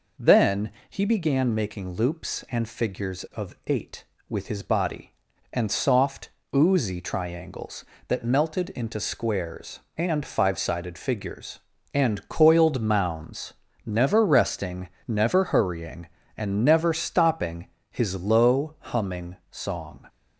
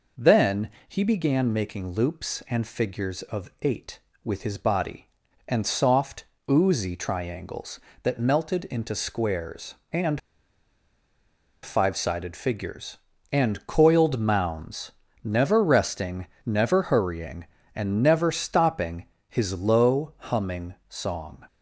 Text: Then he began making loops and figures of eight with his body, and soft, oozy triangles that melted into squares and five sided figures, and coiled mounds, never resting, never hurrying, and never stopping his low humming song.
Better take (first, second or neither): first